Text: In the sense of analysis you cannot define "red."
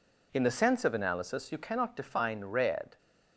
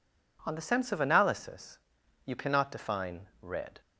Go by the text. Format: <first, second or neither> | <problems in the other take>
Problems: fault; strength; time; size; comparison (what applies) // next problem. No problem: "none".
first | says "On" for "In"; at 0.4 s // pauses between "analysis" and "you"; noticeable; at 1.7 s; 0.48 s long // pauses between "define" and "red"; slight; at 3.2 s; 0.16 s long